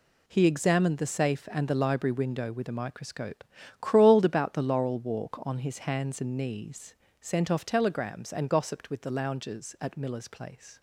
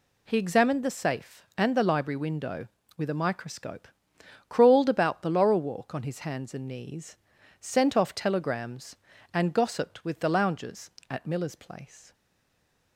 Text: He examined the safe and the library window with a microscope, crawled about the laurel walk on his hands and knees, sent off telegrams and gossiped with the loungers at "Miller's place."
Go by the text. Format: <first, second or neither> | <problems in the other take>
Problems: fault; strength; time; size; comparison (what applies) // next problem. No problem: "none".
first | stays silent after the last word; slight; from 12.1 s on; 0.8 s long